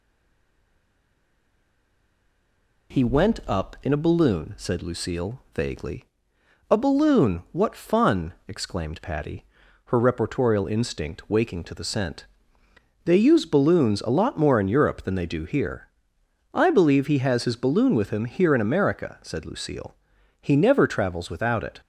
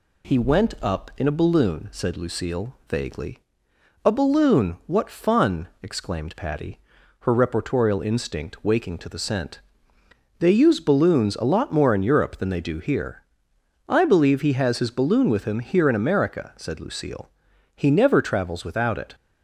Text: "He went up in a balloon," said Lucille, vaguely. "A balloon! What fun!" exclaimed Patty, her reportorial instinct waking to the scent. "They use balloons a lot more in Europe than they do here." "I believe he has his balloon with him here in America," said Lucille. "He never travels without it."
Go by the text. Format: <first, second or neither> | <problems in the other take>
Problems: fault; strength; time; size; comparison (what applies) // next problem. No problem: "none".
second | stays silent before the first word; strong; until 2.9 s; 2.9 s long